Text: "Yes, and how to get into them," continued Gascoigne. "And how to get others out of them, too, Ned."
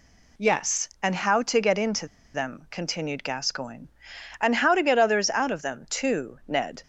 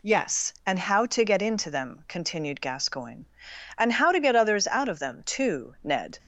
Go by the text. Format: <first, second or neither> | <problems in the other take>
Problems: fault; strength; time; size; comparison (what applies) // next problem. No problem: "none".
second | pauses between "into" and "them"; slight; at 2.0 s; 0.28 s long